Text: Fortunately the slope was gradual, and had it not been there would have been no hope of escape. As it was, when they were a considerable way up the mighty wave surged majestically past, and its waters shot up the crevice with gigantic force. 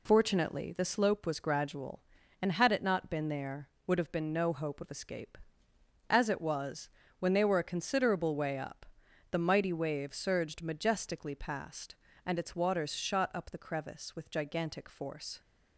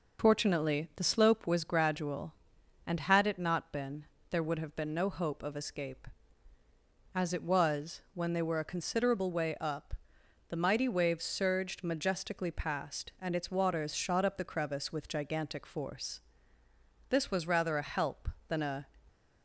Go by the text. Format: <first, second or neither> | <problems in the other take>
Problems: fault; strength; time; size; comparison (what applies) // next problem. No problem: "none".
first | pauses between "been" and "there"; slight; at 4.0 s; 0.24 s long // pauses between "up" and "the"; noticeable; at 9.9 s; 0.56 s long; noticeable in the first // goes on to say "This was rather a help than a"; strong; from 17.0 s on; 1.8 s long